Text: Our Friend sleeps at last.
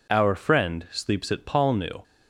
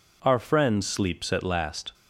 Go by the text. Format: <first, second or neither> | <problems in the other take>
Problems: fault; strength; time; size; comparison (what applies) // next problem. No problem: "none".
second | says "palnu" for "last"; at 1.4 s